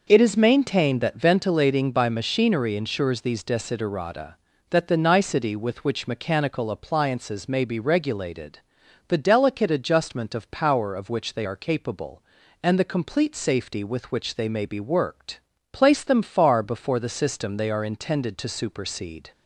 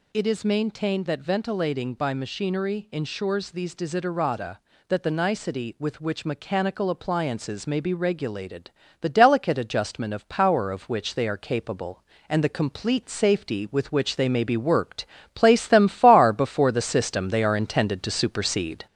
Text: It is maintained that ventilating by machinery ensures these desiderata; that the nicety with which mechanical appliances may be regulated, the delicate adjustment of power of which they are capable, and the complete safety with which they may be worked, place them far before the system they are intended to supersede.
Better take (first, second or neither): first